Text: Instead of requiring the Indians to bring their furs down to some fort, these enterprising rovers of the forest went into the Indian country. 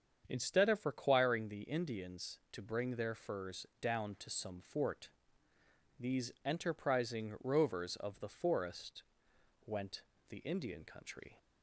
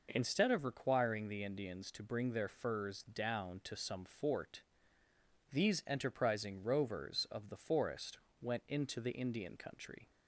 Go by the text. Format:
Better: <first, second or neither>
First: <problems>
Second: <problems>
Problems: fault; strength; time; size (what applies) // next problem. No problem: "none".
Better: second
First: starts louder than the rest; strong; until 1.2 s; 7.5 dB // pauses between "forest" and "went"; noticeable; at 9.0 s; 0.62 s long // skips "into"; at 10.1 s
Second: pauses between "forest" and "went"; slight; at 8.1 s; 0.24 s long